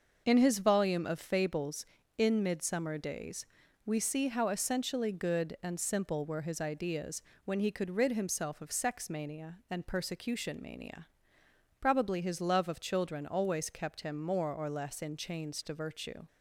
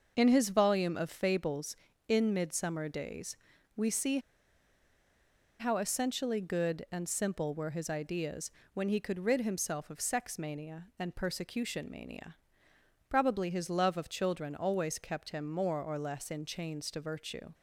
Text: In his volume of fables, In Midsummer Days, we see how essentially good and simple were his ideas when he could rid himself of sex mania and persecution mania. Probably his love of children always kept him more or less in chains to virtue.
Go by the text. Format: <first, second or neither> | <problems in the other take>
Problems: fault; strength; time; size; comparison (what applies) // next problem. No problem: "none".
first | starts louder than the rest; noticeable; until 1.1 s; 6 dB; noticeable in the first // pauses between "see" and "how"; strong; at 4.1 s; 1.4 s long // pauses between "ideas" and "when"; slight; at 8.5 s; 0.24 s long; slight in the first